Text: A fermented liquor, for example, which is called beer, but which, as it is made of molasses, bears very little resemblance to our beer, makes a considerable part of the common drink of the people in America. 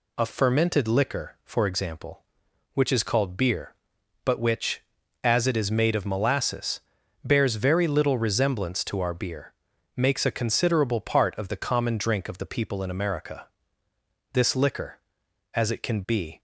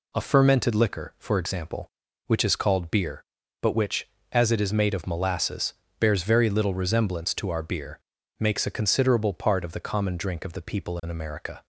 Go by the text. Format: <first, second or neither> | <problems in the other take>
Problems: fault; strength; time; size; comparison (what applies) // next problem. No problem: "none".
second | goes on to say "This liquor as it can be"; strong; from 14.3 s on; 2.0 s long